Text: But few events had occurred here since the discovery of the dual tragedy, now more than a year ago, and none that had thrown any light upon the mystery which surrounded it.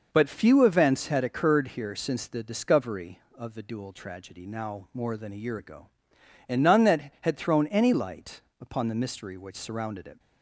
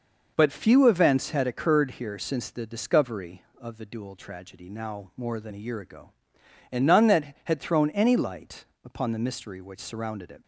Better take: neither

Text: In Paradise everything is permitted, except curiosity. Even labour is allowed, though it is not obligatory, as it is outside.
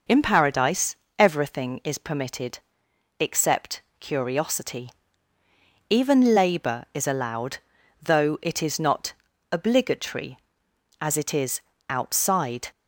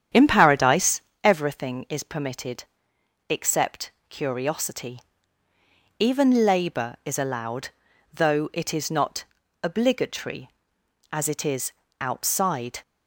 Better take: first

